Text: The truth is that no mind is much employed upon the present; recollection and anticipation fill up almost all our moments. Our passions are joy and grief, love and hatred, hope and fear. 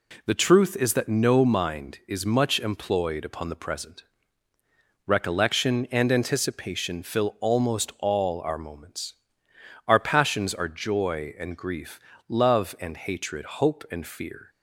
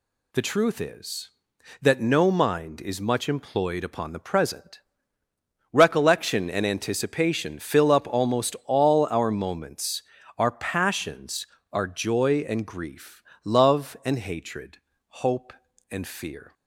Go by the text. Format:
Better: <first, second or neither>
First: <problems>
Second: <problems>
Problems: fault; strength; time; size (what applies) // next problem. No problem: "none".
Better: second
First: skips "up"; at 7.3 s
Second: none